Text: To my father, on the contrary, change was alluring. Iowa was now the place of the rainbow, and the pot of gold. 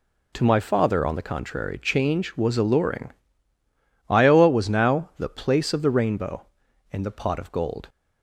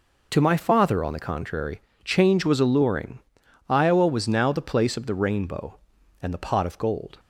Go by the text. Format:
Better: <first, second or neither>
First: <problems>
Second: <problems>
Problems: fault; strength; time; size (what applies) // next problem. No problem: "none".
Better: neither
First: none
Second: none